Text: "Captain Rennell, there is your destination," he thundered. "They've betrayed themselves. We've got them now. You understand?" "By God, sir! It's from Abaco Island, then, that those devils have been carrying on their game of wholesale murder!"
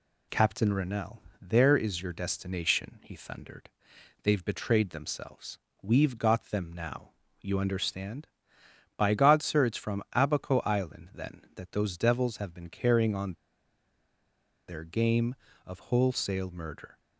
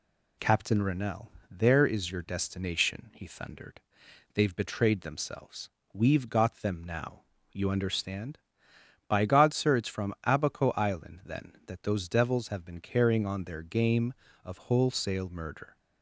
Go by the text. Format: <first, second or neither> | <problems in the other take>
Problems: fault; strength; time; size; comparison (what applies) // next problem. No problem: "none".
second | pauses between "on" and "their"; strong; at 13.3 s; 1.3 s long